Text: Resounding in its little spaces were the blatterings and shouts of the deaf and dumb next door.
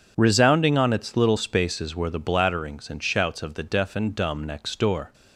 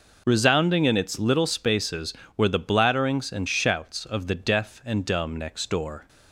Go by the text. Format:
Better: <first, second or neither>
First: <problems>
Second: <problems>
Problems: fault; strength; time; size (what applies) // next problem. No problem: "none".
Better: second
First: says "on" for "in"; at 0.7 s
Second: none